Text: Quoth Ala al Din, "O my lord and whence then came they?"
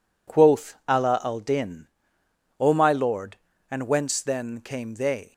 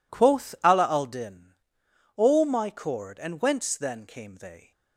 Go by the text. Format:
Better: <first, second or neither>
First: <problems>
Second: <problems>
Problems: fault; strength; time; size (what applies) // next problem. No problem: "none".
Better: first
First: none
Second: says "cord" for "lord"; at 2.7 s